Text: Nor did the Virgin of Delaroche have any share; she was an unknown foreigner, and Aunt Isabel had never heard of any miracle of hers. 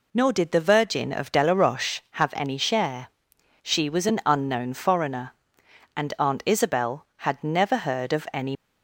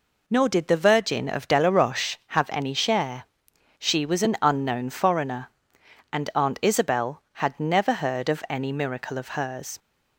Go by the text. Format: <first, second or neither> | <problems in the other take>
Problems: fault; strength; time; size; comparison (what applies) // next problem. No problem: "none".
second | stops before "miracle of hers"; at 8.5 s